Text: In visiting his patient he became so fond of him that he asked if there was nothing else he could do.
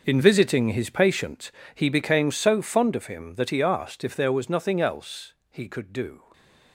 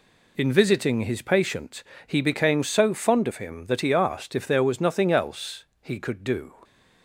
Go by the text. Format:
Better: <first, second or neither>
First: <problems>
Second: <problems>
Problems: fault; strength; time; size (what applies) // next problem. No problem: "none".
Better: second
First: gets quieter; strong; throughout; 14 dB // pauses between "patient" and "he"; slight; at 1.4 s; 0.26 s long // pauses between "else" and "he"; slight; at 5.3 s; 0.18 s long // stays silent after the last word; slight; from 6.1 s on; 0.6 s long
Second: pauses between "patient" and "he"; slight; at 1.8 s; 0.26 s long // pauses between "else" and "he"; slight; at 5.6 s; 0.18 s long